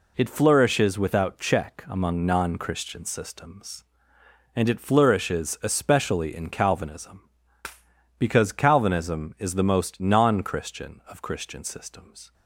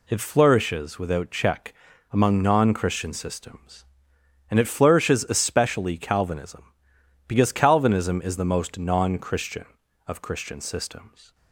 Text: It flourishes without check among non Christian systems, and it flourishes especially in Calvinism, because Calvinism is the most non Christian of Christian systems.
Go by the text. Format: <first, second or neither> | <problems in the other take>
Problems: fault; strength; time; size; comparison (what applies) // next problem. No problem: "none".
first | pauses between "check" and "among"; at 1.7 s; 0.40 s long // skips "in"; at 5.9 s